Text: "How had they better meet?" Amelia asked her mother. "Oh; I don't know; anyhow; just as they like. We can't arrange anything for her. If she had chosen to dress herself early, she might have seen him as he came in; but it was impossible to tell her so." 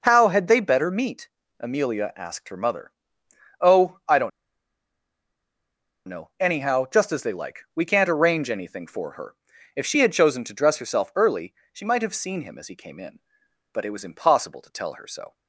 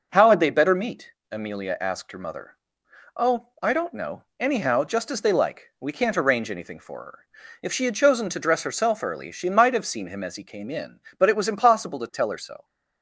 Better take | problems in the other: second | pauses between "don't" and "know"; strong; at 4.3 s; 1.7 s long

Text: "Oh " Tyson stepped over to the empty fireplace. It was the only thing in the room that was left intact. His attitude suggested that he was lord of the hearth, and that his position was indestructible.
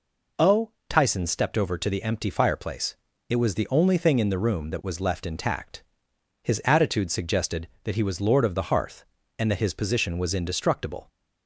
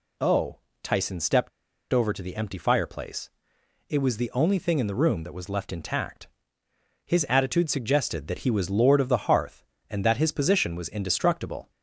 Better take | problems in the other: first | pauses between "stepped" and "over"; at 1.4 s; 0.43 s long

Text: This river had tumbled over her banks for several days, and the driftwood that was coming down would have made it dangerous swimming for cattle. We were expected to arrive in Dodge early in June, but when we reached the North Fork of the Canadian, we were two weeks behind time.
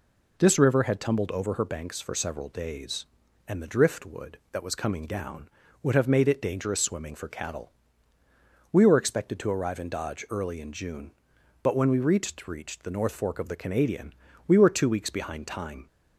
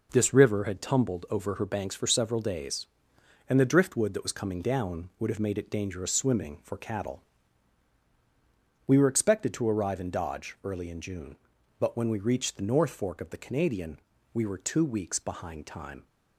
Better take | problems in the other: second | says "reached" twice; at 12.4 s

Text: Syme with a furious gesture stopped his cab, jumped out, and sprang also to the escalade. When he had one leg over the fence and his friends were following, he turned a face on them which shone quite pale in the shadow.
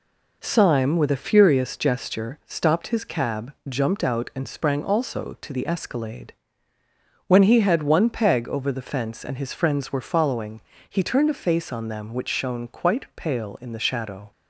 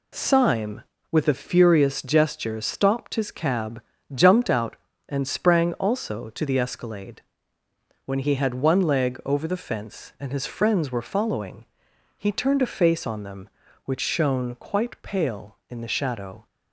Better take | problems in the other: second | says "peg" for "leg"; at 8.0 s

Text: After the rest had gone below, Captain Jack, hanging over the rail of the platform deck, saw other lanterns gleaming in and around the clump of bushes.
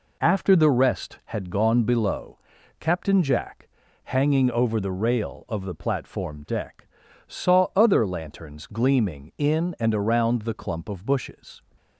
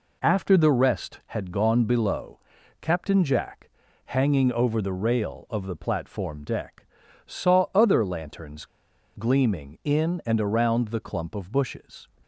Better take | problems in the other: first | pauses between "lanterns" and "gleaming"; noticeable; at 8.6 s; 0.50 s long

